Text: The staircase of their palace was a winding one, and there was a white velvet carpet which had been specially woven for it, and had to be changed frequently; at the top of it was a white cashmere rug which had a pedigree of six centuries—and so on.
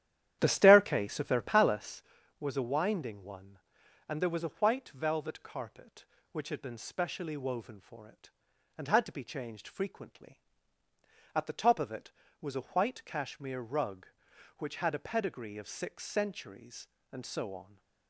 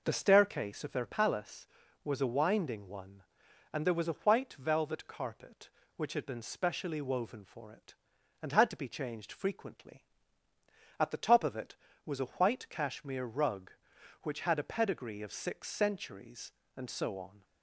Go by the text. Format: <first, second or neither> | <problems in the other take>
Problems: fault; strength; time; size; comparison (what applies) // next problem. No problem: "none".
second | starts louder than the rest; strong; until 2.2 s; 11 dB